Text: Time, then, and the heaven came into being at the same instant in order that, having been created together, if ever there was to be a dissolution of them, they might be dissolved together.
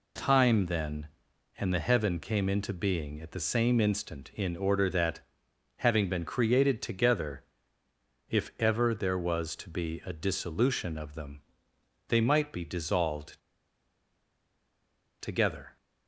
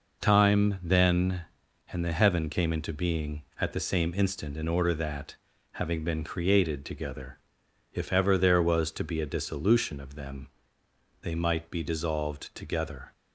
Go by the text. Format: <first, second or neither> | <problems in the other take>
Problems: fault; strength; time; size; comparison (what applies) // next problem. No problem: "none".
second | pauses between "dissolved" and "together"; strong; at 13.4 s; 1.8 s long